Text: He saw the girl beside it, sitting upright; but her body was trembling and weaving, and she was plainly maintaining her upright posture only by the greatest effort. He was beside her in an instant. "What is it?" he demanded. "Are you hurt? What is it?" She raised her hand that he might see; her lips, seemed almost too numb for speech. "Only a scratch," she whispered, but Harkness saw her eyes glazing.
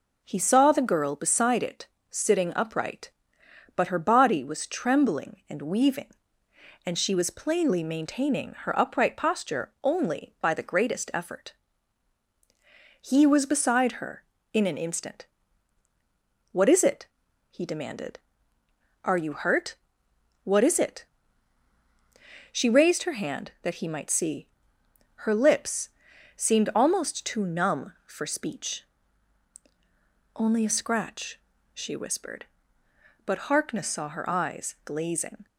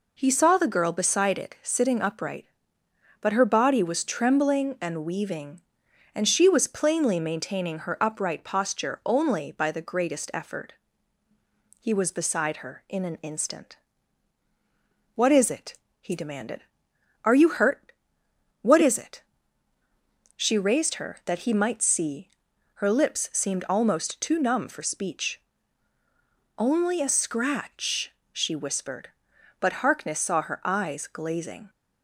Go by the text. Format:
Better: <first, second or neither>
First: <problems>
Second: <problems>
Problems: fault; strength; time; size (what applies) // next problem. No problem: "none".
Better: first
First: none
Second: skips "hand"; at 21.2 s